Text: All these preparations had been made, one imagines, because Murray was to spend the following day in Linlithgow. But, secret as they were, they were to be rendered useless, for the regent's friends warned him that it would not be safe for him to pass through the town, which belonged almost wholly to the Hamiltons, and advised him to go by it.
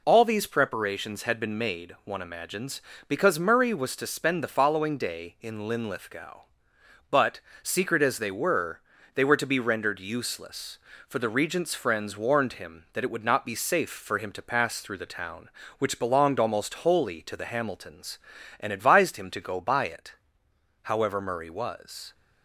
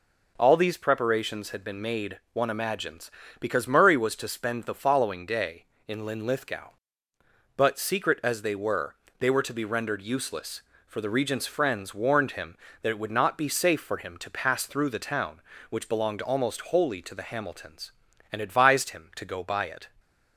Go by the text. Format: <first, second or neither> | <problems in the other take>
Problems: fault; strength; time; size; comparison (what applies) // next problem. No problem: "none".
second | goes on to say "However Murray was"; noticeable; from 20.8 s on; 1.3 s long